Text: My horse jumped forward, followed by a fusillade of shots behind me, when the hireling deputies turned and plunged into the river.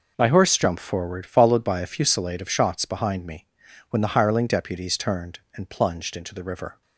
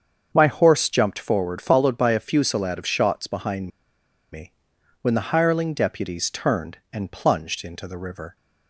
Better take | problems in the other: first | starts louder than the rest; until 1.3 s; 7 dB // pauses between "behind" and "me"; noticeable; at 3.6 s; 0.64 s long

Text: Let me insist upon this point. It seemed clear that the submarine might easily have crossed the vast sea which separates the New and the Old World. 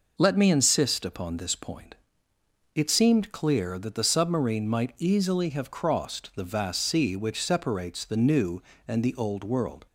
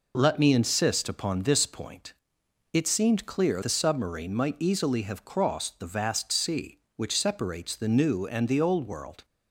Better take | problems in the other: first | skips "that"; at 3.6 s

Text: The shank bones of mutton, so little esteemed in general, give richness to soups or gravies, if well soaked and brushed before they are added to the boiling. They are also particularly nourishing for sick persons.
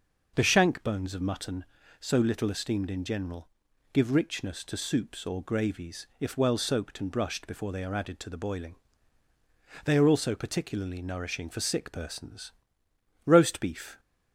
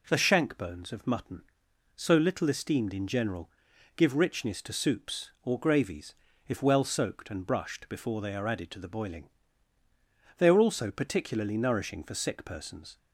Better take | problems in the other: second | goes on to say "Roast beef"; noticeable; from 13.2 s on; 0.74 s long

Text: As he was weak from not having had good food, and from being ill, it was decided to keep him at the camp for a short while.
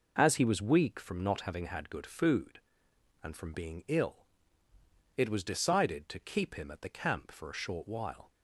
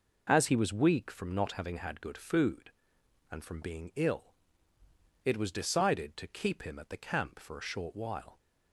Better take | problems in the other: neither | none

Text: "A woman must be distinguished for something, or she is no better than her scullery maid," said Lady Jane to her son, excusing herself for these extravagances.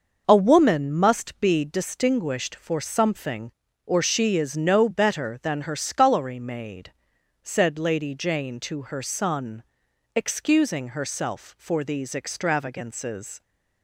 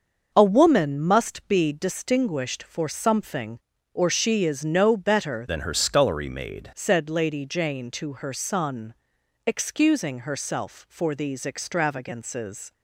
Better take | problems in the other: first | starts louder than the rest; until 1.3 s; 6 dB; noticeable in the first // changes voice from "than" to "maid"; from 5.4 to 6.6 s; 1.2 s long

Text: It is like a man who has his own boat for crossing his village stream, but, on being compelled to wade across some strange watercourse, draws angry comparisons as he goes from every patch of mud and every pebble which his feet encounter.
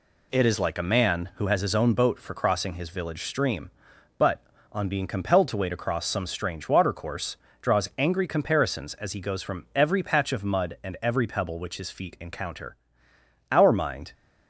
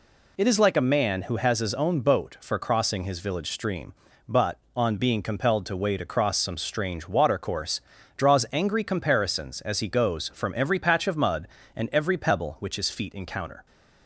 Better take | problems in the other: second | goes on to say "Our mind"; noticeable; from 13.5 s on; 0.62 s long

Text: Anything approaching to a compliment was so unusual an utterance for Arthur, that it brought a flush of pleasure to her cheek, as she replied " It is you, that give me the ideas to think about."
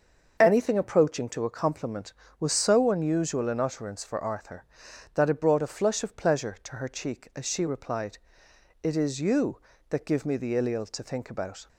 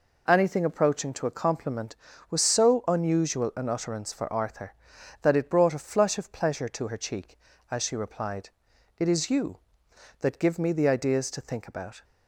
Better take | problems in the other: second | starts louder than the rest; until 1.4 s; 6.5 dB // says "ileal" for "ideas"; at 10.5 s

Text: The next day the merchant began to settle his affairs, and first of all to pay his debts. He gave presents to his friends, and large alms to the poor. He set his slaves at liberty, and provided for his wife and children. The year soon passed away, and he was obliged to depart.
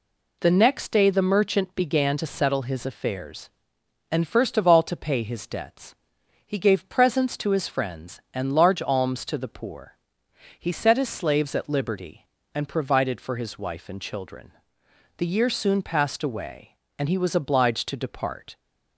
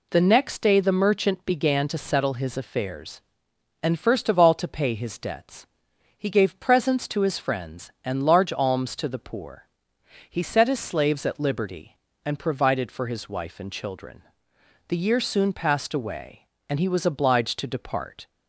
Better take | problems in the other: neither | none

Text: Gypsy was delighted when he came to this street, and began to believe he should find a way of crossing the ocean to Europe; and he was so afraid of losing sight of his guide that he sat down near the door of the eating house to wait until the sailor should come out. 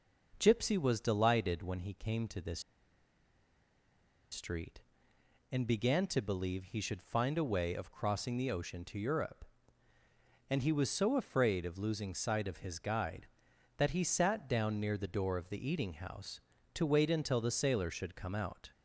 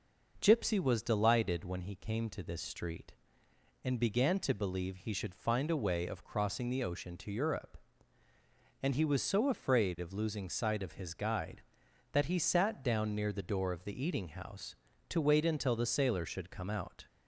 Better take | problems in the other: second | pauses between "this" and "street"; strong; at 2.5 s; 1.7 s long

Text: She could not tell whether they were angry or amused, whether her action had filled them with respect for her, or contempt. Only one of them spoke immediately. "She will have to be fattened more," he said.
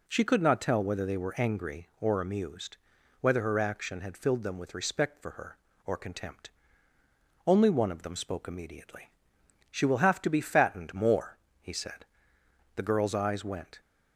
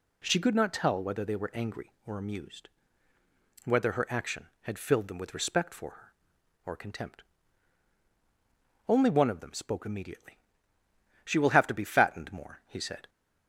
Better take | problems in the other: second | goes on to say "The girl's eyes went"; noticeable; from 12.7 s on; 1.0 s long

